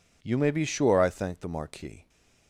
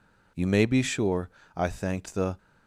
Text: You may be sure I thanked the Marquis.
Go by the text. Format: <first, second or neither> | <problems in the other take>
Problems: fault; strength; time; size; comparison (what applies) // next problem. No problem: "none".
first | pauses between "sure" and "I"; slight; at 1.2 s; 0.26 s long // stops before "Marquis"; at 2.3 s